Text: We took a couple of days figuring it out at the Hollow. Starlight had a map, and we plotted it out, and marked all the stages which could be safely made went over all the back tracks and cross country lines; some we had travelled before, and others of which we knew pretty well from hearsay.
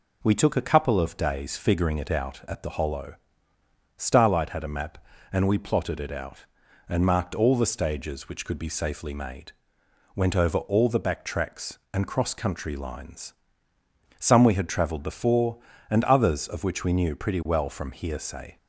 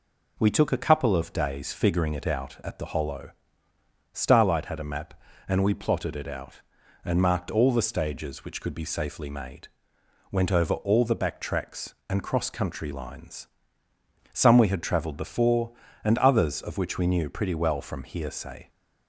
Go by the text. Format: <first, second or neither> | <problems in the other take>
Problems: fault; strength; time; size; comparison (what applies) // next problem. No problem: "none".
neither | pauses between "made" and "went"; noticeable; the same in both